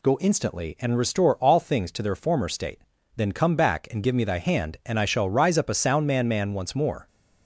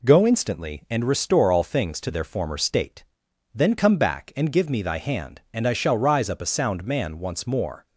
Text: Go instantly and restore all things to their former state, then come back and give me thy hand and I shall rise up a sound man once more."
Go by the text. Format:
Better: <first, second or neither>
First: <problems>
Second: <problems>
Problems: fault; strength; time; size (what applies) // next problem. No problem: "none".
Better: second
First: says "man" twice; at 6.2 s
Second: none